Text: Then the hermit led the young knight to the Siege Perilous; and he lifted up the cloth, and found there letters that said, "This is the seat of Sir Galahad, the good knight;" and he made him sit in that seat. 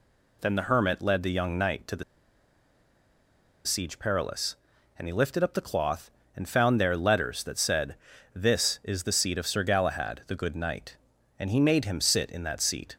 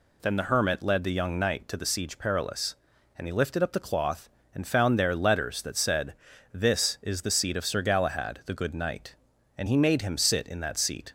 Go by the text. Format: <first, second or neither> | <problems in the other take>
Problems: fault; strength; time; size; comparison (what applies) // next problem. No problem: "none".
second | pauses between "the" and "Siege"; strong; at 2.0 s; 1.6 s long